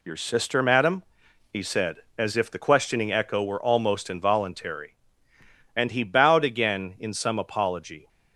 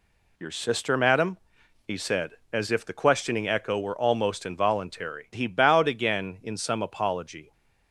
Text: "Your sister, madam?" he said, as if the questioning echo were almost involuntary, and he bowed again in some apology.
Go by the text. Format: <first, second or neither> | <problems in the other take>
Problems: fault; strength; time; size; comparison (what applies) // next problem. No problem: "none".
first | skips "and"; at 5.3 s